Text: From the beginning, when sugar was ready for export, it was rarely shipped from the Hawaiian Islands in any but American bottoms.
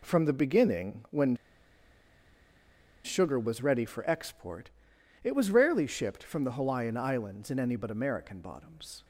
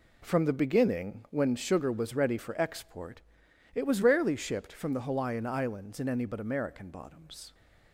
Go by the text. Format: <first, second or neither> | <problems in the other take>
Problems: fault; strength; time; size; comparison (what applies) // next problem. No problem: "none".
second | pauses between "when" and "sugar"; strong; at 1.3 s; 1.6 s long